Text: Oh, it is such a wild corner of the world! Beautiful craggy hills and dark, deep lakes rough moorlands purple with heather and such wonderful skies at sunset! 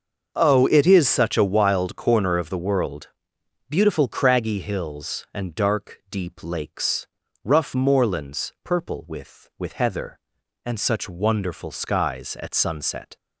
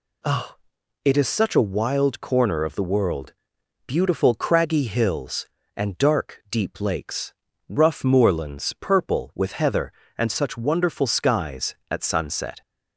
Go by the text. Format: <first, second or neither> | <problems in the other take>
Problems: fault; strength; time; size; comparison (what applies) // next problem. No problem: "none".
second | starts louder than the rest; until 1.3 s; 6.5 dB // pauses between "lakes" and "rough"; at 7.0 s; 0.38 s long; also in the second // says "with" twice; at 9.5 s